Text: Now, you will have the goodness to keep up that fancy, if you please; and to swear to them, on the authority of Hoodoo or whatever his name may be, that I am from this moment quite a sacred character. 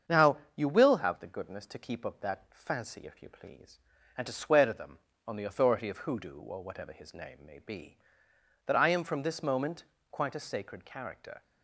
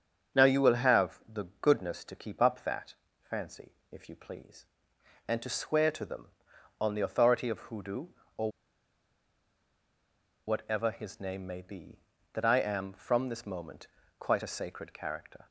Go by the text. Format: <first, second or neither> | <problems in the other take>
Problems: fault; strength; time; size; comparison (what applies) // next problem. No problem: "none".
first | starts louder than the rest; until 1.6 s; 7 dB; strong in the first // pauses between "that" and "fancy"; slight; at 2.9 s; 0.34 s long // pauses between "or" and "whatever"; strong; at 8.5 s; 1.9 s long // pauses between "moment" and "quite"; slight; at 13.8 s; 0.32 s long; slight in the first